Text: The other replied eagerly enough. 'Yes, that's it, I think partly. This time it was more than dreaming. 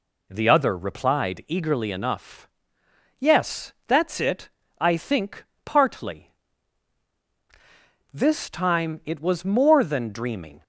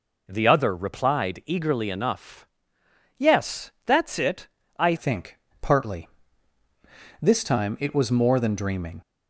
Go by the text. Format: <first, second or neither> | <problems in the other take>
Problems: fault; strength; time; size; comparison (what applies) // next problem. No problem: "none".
first | changes voice at "think"; from 4.9 s on; 4.1 s long // pauses between "think" and "partly"; slight; at 5.3 s; 0.24 s long; slight in the first